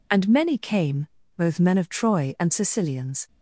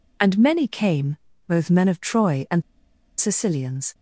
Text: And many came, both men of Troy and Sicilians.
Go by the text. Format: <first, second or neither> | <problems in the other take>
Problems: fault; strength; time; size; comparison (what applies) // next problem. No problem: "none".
first | pauses between "and" and "Sicilians"; noticeable; at 2.6 s; 0.55 s long